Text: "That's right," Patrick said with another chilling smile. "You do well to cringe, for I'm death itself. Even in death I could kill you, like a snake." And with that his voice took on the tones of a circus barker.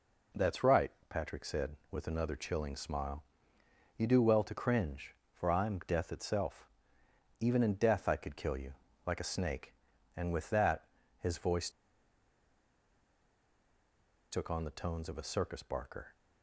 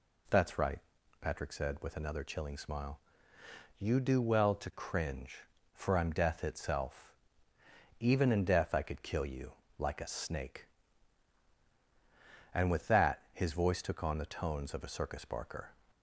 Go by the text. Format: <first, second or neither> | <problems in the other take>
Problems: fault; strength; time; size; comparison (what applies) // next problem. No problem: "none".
second | pauses between "that" and "his"; slight; at 10.8 s; 0.32 s long // pauses between "voice" and "took"; strong; at 11.7 s; 2.6 s long